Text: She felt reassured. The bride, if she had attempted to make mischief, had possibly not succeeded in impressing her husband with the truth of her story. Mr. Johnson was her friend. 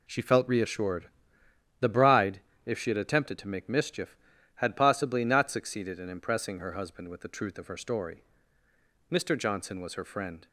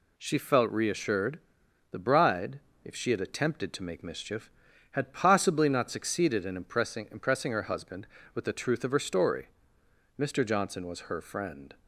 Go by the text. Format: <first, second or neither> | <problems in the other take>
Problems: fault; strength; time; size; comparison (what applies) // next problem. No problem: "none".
first | says "impressing" twice; at 7.1 s